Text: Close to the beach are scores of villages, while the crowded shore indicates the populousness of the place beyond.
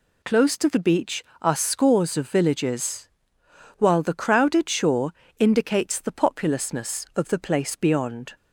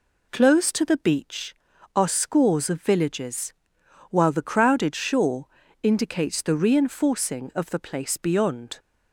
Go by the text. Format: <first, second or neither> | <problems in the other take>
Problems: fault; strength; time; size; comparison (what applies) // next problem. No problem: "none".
first | pauses between "shore" and "indicates"; slight; at 5.4 s; 0.36 s long; slight in the first // says "reinforcing" for "populousness"; at 6.5 s